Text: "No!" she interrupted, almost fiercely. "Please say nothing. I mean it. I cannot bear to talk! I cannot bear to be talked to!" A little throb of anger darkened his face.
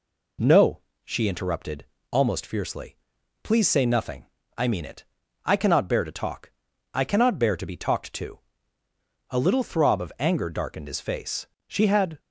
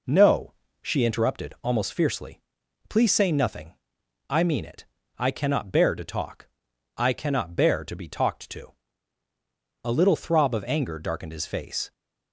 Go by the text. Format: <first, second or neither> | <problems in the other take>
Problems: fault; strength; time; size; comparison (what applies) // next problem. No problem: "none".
second | goes on to say "She had"; from 11.6 s on; 0.52 s long